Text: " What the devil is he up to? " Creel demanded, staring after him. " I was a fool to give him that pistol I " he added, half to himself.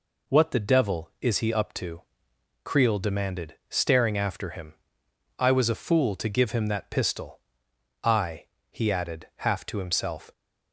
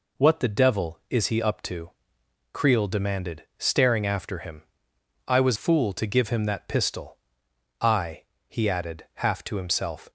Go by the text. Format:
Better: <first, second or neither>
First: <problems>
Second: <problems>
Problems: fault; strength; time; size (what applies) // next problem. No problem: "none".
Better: first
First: pauses between "pistol" and "I"; noticeable; at 7.3 s; 0.64 s long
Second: skips "a"; at 5.5 s // pauses between "pistol" and "I"; noticeable; at 7.1 s; 0.64 s long